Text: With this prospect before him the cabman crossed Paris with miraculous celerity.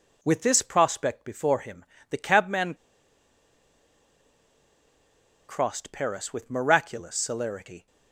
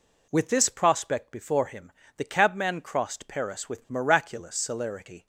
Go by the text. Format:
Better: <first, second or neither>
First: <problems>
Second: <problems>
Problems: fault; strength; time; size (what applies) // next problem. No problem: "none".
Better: second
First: pauses between "him" and "the"; slight; at 1.8 s; 0.28 s long // pauses between "cabman" and "crossed"; strong; at 2.7 s; 2.7 s long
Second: pauses between "him" and "the"; slight; at 1.8 s; 0.28 s long